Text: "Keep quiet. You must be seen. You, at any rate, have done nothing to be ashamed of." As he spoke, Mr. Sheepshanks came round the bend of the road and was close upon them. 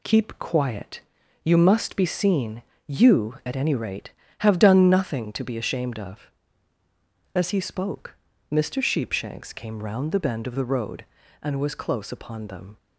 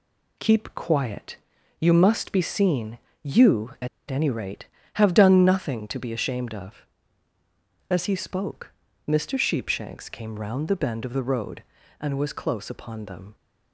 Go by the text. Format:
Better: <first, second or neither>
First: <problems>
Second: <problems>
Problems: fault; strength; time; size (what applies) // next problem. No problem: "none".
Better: first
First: none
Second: pauses between "at" and "any"; slight; at 3.8 s; 0.22 s long